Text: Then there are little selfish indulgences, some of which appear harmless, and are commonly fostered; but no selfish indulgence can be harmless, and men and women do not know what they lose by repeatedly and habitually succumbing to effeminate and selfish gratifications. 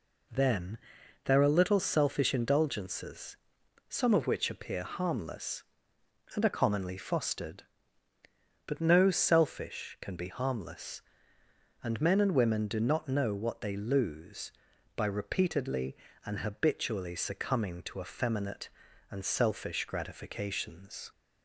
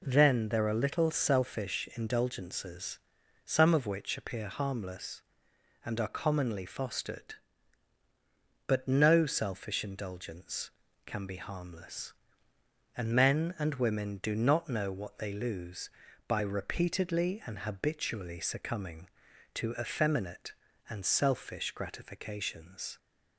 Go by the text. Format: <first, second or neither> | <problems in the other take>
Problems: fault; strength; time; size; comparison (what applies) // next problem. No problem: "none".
second | pauses between "Then" and "there"; noticeable; at 0.7 s; 0.46 s long // skips "indulgence"; at 9.9 s